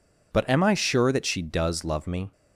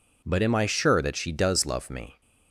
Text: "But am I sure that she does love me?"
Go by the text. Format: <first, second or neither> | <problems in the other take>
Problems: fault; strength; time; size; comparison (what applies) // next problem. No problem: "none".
neither | none